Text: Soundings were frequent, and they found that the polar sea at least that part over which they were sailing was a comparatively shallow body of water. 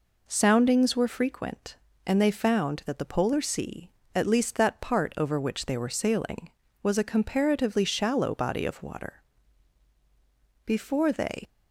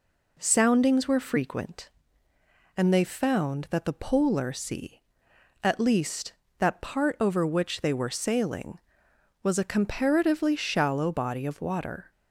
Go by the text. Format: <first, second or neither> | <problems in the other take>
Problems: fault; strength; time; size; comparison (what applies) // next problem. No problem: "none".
second | goes on to say "Before they"; noticeable; from 10.6 s on; 0.84 s long